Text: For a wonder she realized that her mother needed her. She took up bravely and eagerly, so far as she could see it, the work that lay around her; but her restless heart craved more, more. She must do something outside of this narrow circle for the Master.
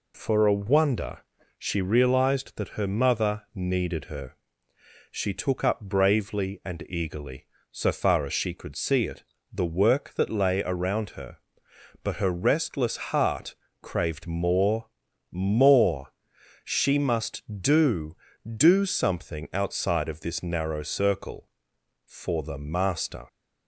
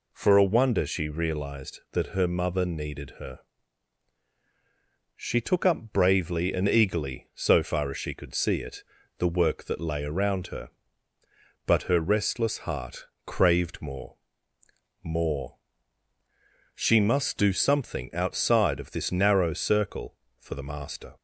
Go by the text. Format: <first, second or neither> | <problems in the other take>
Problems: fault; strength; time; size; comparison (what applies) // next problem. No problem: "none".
second | pauses between "wonder" and "she"; slight; at 1.1 s; 0.36 s long // pauses between "restless" and "heart"; slight; at 12.9 s; 0.16 s long // pauses between "heart" and "craved"; slight; at 13.5 s; 0.26 s long; slight in the second // says "do" twice; at 18.4 s